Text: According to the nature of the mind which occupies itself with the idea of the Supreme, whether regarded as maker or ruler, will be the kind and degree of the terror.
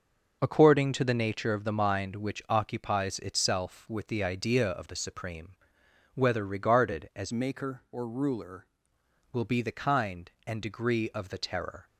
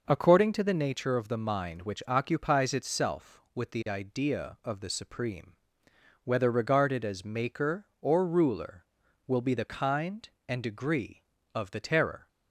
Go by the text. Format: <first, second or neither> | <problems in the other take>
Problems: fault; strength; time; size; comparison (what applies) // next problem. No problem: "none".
second | changes voice from "maker" to "ruler"; from 7.3 to 8.6 s; 1.3 s long